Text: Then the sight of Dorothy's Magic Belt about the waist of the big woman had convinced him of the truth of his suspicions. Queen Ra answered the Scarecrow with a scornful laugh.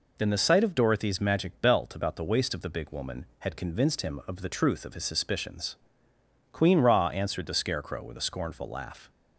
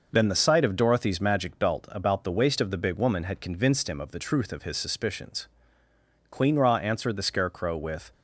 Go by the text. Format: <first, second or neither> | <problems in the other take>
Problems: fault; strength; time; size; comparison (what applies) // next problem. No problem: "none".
first | stops before "a scornful laugh"; at 8.1 s